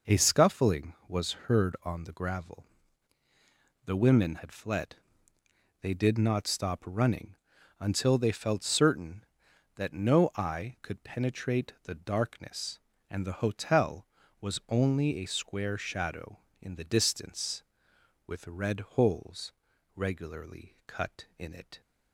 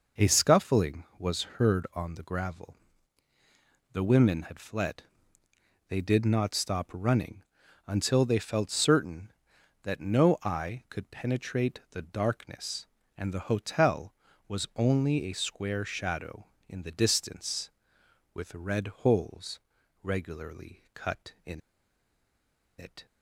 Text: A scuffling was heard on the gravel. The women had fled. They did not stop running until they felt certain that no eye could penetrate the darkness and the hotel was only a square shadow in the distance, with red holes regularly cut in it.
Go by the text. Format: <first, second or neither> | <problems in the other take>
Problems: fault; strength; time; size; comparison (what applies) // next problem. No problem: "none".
first | pauses between "was" and "heard"; slight; at 1.4 s; 0.16 s long; slight in the first // pauses between "running" and "until"; at 7.4 s; 0.42 s long; also in the first // pauses between "red" and "holes"; slight; at 18.8 s; 0.16 s long; slight in the first // pauses between "holes" and "regularly"; at 19.5 s; 0.42 s long; also in the first // pauses between "in" and "it"; at 21.5 s; 1.1 s long